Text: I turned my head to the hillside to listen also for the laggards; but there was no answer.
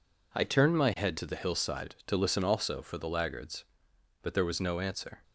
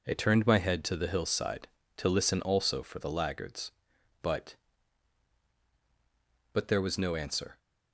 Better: first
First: none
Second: says "but" twice; at 6.5 s

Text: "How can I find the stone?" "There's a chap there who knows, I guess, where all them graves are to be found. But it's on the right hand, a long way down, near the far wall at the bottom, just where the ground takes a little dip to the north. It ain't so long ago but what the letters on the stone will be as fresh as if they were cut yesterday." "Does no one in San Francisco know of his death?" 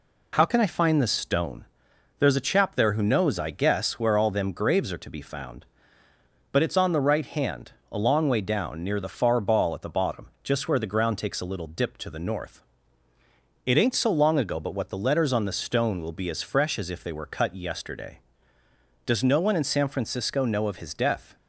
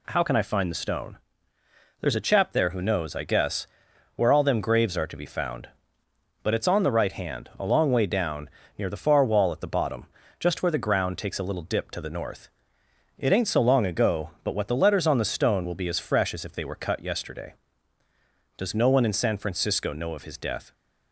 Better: second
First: says "ball" for "wall"; at 9.3 s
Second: none

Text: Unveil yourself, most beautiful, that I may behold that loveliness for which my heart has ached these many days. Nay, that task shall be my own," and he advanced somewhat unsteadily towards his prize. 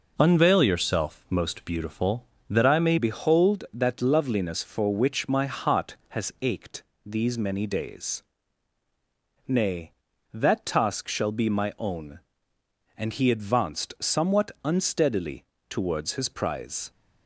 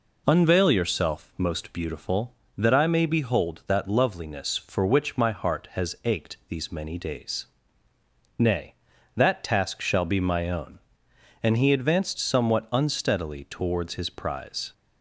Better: second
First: changes voice at "behold"; from 2.9 s on; 14.0 s long // pauses between "ached" and "these"; slight; at 6.8 s; 0.22 s long // pauses between "unsteadily" and "towards"; slight; at 15.4 s; 0.24 s long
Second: none

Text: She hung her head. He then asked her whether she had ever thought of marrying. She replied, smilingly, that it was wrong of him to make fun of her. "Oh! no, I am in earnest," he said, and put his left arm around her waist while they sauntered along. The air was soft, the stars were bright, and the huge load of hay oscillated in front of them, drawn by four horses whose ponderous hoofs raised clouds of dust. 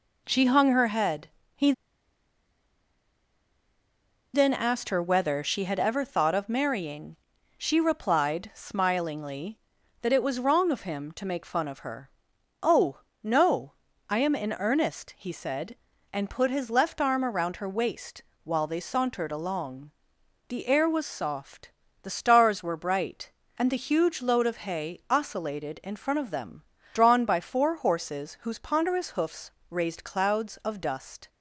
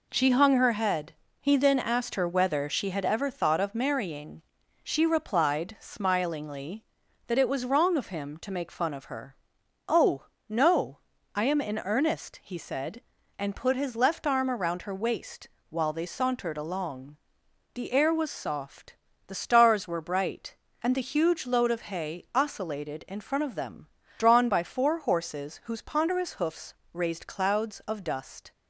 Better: second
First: pauses between "He" and "then"; strong; at 1.7 s; 2.6 s long // pauses between "waist" and "while"; slight; at 18.2 s; 0.20 s long // pauses between "hoofs" and "raised"; slight; at 29.5 s; 0.18 s long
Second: pauses between "waist" and "while"; slight; at 15.4 s; 0.20 s long // pauses between "hoofs" and "raised"; slight; at 26.7 s; 0.18 s long

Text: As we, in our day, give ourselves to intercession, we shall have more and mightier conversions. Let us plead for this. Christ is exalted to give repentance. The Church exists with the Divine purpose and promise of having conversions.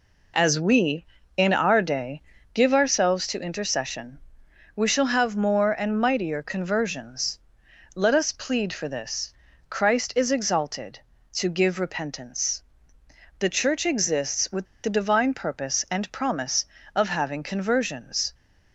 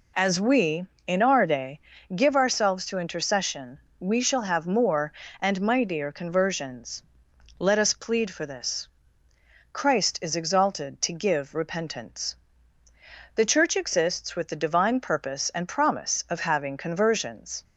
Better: second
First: pauses between "with" and "the"; slight; at 14.6 s; 0.18 s long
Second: none

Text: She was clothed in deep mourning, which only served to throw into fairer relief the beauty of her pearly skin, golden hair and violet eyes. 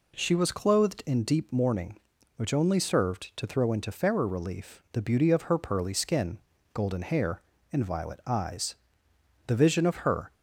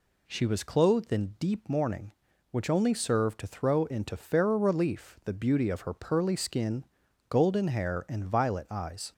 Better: second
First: goes on to say "The vision of her"; noticeable; from 9.4 s on; 0.86 s long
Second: none

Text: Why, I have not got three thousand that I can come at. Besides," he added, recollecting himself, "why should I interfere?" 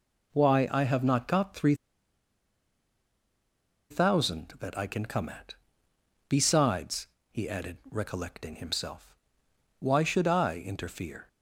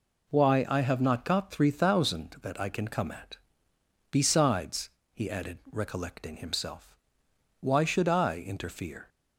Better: second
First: pauses between "three" and "thousand"; strong; at 1.7 s; 2.1 s long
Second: none

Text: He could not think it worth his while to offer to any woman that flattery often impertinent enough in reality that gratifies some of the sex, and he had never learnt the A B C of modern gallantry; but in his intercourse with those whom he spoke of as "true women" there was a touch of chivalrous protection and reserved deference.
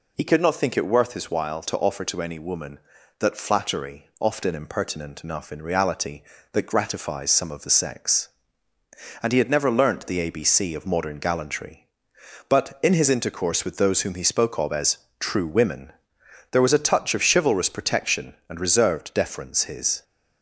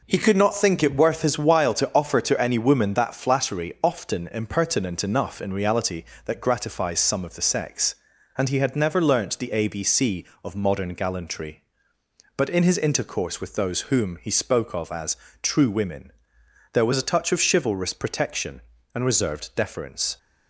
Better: second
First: pauses between "as" and "true"; slight; at 14.9 s; 0.24 s long // pauses between "women" and "there"; noticeable; at 15.9 s; 0.60 s long // goes on to say "His"; slight; from 19.6 s on; 0.40 s long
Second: pauses between "as" and "true"; slight; at 15.1 s; 0.26 s long // pauses between "women" and "there"; noticeable; at 16.1 s; 0.62 s long

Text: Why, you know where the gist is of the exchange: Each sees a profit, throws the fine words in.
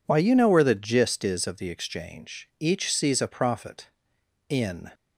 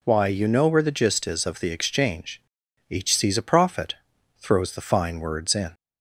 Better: second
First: skips "throws the fine words"; at 4.1 s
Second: none

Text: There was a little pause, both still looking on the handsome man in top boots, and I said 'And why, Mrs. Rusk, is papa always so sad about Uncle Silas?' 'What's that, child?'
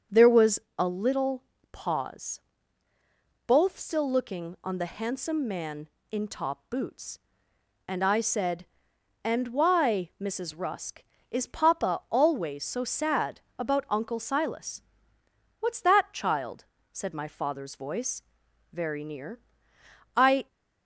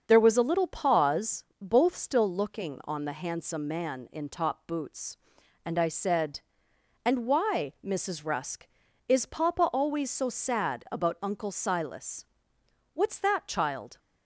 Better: second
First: starts louder than the rest; until 1.3 s; 6.5 dB // pauses between "was" and "a"; slight; at 0.5 s; 0.20 s long // pauses between "little" and "pause"; slight; at 1.4 s; 0.28 s long // pauses between "sad" and "about"; slight; at 13.4 s; 0.18 s long // goes on to say "said my father's voice very near I"; strong; from 16.9 s on; 3.5 s long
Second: starts louder than the rest; until 1.0 s; 6.5 dB

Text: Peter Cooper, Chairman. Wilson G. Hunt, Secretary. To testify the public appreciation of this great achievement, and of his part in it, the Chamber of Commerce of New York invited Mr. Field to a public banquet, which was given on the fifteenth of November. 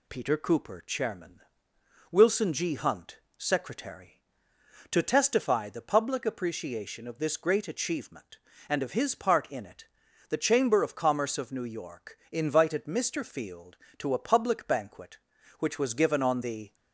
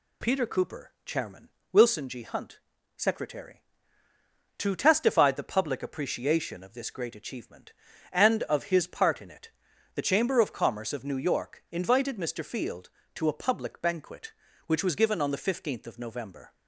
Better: second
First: stops before "fifteenth of November"; at 16.7 s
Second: none

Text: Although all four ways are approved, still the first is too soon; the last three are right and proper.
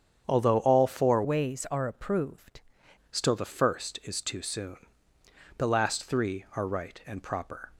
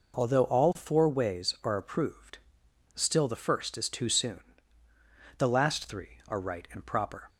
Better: second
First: starts louder than the rest; strong; until 1.2 s; 8 dB // changes voice from "ways" to "approved"; from 1.2 to 2.6 s; 1.4 s long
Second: none

